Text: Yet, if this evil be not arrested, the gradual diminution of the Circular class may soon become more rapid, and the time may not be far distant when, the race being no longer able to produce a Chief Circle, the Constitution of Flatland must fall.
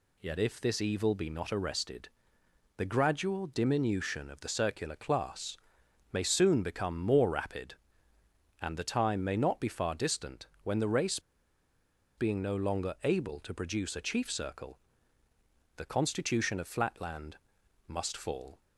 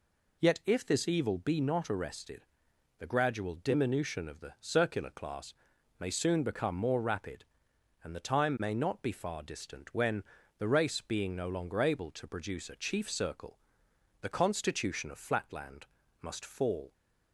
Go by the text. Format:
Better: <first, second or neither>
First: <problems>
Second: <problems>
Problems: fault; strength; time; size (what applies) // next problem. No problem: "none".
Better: second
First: pauses between "class" and "may"; noticeable; at 5.5 s; 0.56 s long // pauses between "distant" and "when"; slight; at 10.4 s; 0.16 s long // pauses between "race" and "being"; noticeable; at 11.1 s; 0.97 s long // pauses between "Flatland" and "must"; noticeable; at 17.3 s; 0.50 s long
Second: pauses between "class" and "may"; noticeable; at 5.5 s; 0.46 s long // pauses between "Flatland" and "must"; at 15.8 s; 0.38 s long